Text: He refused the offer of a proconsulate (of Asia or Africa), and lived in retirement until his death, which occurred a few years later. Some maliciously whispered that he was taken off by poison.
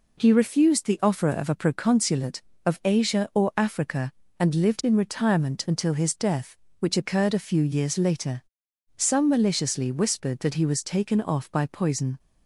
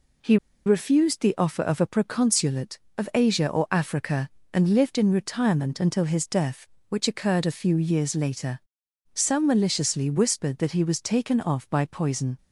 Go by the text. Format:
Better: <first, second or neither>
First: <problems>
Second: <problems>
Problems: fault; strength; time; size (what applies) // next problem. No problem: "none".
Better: first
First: none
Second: pauses between "He" and "refused"; slight; at 0.3 s; 0.30 s long